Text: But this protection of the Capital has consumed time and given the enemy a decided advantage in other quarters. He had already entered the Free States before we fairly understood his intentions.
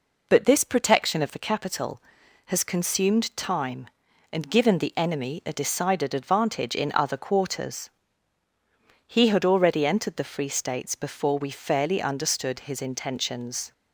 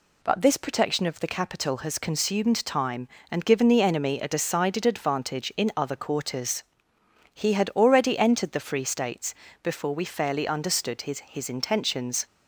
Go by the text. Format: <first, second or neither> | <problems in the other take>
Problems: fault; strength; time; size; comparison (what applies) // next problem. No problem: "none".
first | pauses between "States" and "before"; slight; at 9.3 s; 0.30 s long // says "his" twice; at 11.1 s